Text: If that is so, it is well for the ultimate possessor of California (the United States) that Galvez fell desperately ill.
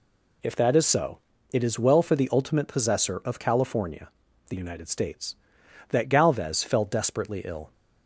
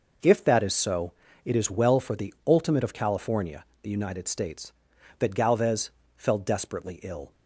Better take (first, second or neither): first